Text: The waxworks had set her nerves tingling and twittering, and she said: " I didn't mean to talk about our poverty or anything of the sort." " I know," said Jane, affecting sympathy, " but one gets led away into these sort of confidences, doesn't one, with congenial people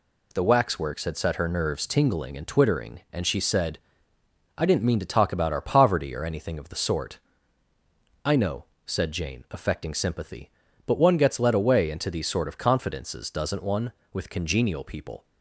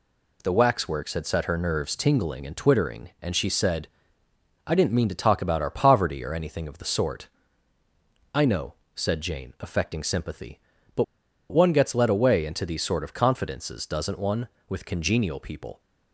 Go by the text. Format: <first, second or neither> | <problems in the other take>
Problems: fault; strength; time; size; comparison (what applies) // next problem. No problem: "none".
first | pauses between "but" and "one"; noticeable; at 11.0 s; 0.47 s long